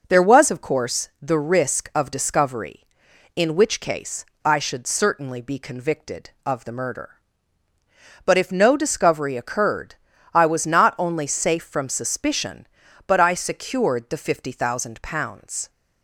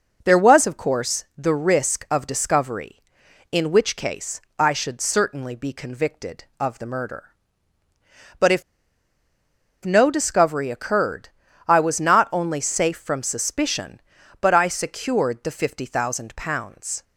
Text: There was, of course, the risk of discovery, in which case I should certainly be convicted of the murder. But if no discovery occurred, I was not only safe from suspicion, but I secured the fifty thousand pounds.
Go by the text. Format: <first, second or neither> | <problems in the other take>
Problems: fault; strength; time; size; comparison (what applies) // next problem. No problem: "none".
first | pauses between "case" and "I"; slight; at 4.3 s; 0.20 s long; slight in the first // pauses between "if" and "no"; at 8.6 s; 1.2 s long